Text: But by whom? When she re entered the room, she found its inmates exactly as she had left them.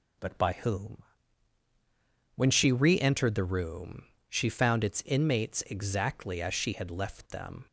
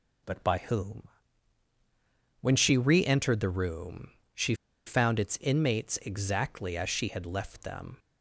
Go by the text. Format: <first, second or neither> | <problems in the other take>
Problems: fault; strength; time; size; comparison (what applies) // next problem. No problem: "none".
first | pauses between "she" and "found"; slight; at 4.5 s; 0.31 s long